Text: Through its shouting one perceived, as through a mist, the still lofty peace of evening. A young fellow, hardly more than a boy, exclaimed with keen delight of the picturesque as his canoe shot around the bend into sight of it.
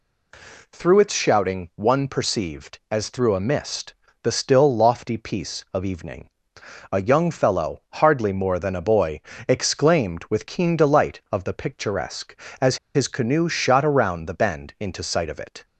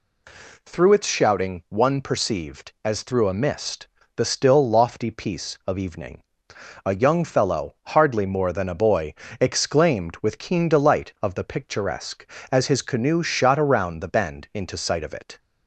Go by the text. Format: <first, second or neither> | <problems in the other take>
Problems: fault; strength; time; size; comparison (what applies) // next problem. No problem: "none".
second | pauses between "as" and "his"; slight; at 12.7 s; 0.19 s long